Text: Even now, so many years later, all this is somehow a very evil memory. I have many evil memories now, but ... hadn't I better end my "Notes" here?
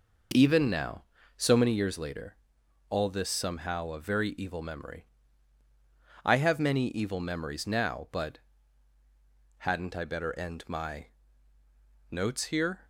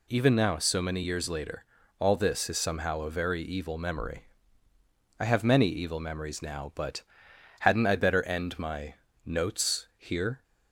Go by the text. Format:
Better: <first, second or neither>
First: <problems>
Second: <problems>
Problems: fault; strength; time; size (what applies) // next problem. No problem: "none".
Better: second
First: skips "is"; at 3.2 s // pauses between "my" and "Notes"; at 11.0 s; 1.0 s long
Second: pauses between "my" and "Notes"; slight; at 8.9 s; 0.30 s long